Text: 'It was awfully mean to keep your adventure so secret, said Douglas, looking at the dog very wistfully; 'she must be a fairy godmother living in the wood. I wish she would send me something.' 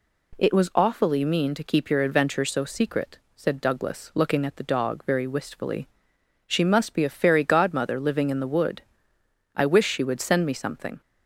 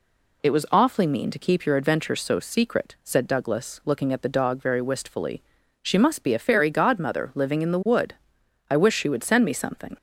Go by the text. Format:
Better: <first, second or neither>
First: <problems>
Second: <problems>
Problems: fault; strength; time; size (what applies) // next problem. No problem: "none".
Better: neither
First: none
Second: none